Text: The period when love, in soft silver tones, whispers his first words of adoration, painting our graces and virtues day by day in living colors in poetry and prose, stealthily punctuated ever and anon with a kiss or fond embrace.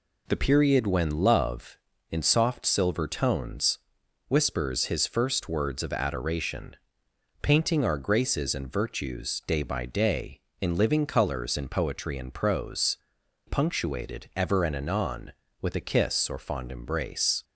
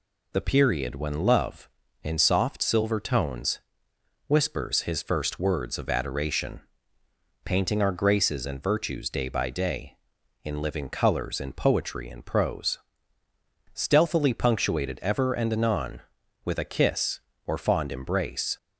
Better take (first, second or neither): second